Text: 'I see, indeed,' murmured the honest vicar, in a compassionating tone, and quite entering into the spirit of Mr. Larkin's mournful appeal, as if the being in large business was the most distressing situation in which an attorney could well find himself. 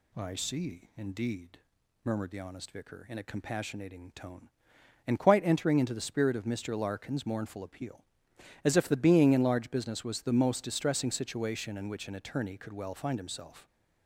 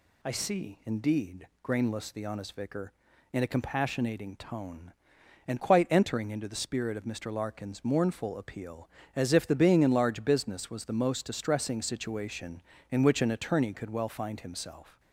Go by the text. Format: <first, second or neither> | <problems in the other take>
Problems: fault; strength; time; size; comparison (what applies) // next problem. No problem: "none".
first | says "grainless" for "murmured"; at 1.6 s